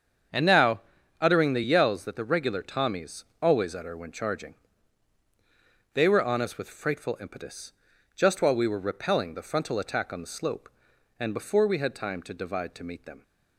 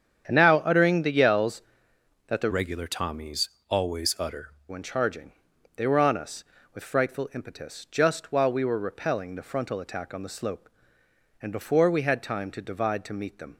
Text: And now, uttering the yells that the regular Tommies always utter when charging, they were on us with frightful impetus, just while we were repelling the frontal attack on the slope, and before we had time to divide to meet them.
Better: first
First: starts louder than the rest; strong; until 1.7 s; 7 dB // pauses between "Tommies" and "always"; slight; at 3.2 s; 0.18 s long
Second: starts louder than the rest; strong; until 1.2 s; 8 dB // changes voice from "regular" to "utter"; from 2.5 to 4.4 s; 1.9 s long // pauses between "Tommies" and "always"; slight; at 3.4 s; 0.22 s long

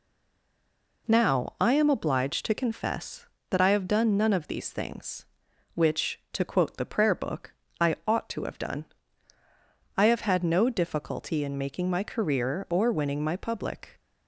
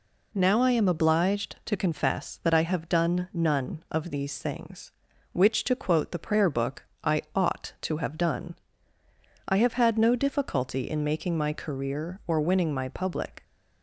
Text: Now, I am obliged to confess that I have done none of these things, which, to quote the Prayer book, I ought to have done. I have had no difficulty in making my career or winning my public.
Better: second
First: stays silent before the first word; until 1.0 s; 1.0 s long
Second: none

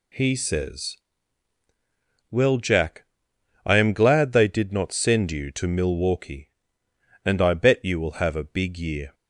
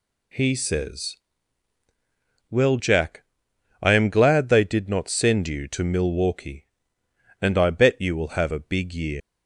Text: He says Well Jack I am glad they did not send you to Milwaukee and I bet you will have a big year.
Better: first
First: pauses between "says" and "Well"; strong; at 0.9 s; 1.3 s long // pauses between "Jack" and "I"; noticeable; at 3.0 s; 0.60 s long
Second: pauses between "says" and "Well"; strong; at 1.1 s; 1.3 s long // pauses between "Jack" and "I"; noticeable; at 3.2 s; 0.58 s long // leaves "year" unfinished; at 9.2 s; 95 ms

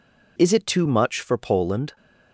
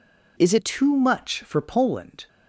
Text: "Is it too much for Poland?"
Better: first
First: none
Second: changes voice at "too"; from 0.6 s on; 1.6 s long

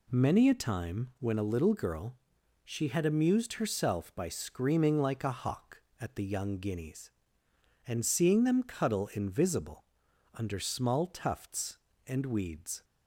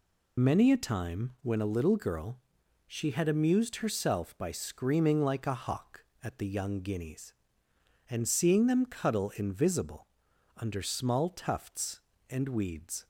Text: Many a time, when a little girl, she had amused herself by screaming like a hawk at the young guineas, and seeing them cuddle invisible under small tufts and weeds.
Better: first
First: pauses between "invisible" and "under"; noticeable; at 9.8 s; 0.48 s long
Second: loses the start of "Many"; at 0.3 s; 70 ms // pauses between "invisible" and "under"; noticeable; at 10.0 s; 0.48 s long

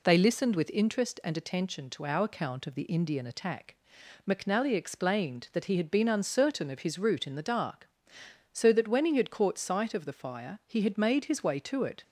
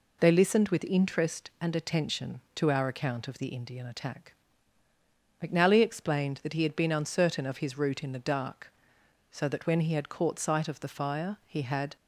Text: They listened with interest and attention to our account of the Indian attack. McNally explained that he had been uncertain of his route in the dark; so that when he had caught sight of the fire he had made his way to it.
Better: first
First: none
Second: stops before "made his way to it"; at 11.9 s

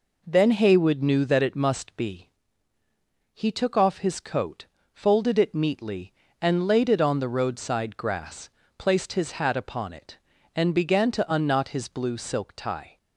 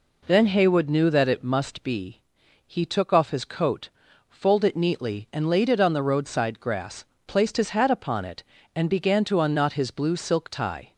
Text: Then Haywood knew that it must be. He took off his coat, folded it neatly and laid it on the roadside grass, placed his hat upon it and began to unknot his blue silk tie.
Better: neither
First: none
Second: none

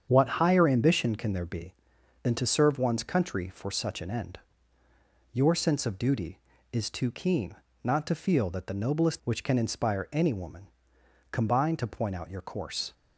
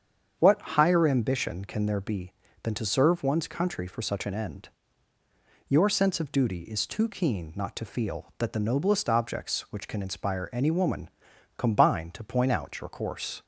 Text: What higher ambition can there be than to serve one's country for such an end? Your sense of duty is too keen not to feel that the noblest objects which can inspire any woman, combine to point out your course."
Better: second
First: starts louder than the rest; strong; until 1.1 s; 8 dB // pauses between "keen" and "not"; slight; at 7.5 s; 0.30 s long // skips "objects"; at 9.2 s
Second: starts louder than the rest; strong; until 1.3 s; 7.5 dB

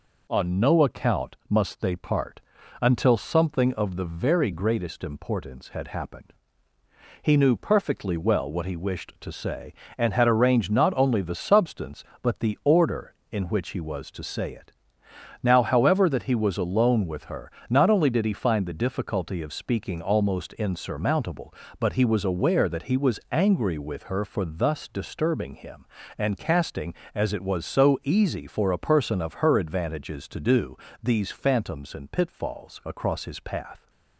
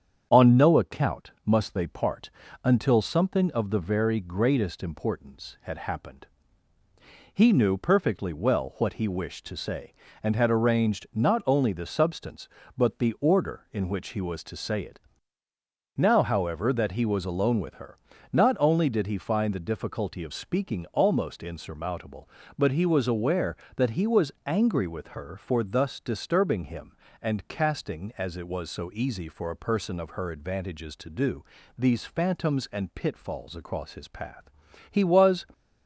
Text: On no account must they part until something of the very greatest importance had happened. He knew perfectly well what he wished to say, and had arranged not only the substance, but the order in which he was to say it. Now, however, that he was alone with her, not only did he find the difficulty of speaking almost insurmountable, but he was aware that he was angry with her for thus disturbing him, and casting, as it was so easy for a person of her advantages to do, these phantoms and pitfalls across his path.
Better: first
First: pauses between "part" and "until"; at 2.4 s; 0.40 s long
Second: starts louder than the rest; strong; until 1.3 s; 8 dB // pauses between "part" and "until"; slight; at 2.3 s; 0.32 s long // goes on to say "He was"; from 34.9 s on; 0.56 s long

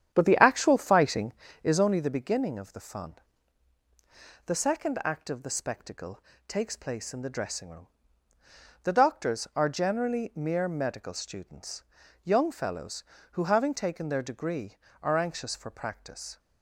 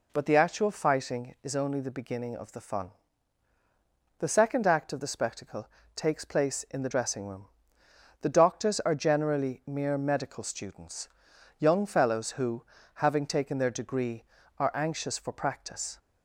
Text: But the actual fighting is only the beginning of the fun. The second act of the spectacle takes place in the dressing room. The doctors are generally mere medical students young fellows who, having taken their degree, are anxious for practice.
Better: second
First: starts louder than the rest; strong; until 1.9 s; 9.5 dB // pauses between "spectacle" and "takes"; slight; at 6.2 s; 0.26 s long // pauses between "students" and "young"; at 11.8 s; 0.42 s long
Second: pauses between "spectacle" and "takes"; slight; at 5.6 s; 0.26 s long // pauses between "students" and "young"; noticeable; at 11.0 s; 0.52 s long

